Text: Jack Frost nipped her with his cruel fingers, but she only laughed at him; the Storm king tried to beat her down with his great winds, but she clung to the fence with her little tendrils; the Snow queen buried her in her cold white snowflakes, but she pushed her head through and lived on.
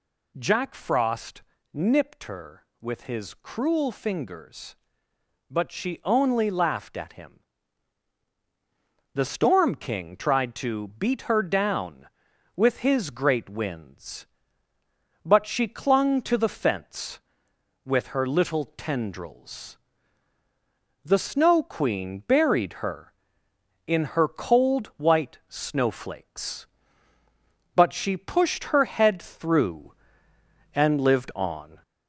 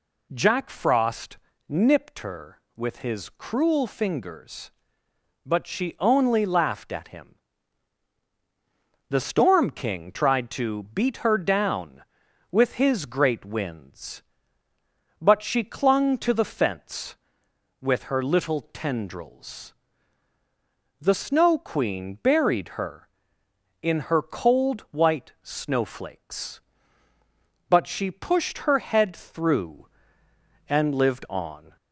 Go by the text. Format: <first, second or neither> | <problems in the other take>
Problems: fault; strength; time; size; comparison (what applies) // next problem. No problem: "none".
second | gets louder; slight; throughout; 2.5 dB // pauses between "Frost" and "nipped"; slight; at 1.4 s; 0.32 s long; slight in the second